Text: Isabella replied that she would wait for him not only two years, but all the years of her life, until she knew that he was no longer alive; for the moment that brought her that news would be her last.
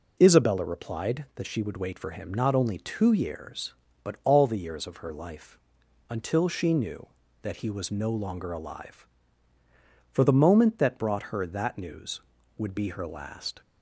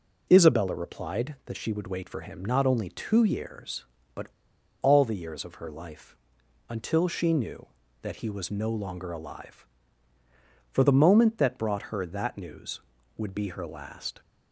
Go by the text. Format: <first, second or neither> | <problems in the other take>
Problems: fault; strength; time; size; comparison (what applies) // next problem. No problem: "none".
first | pauses between "but" and "all"; noticeable; at 4.2 s; 0.56 s long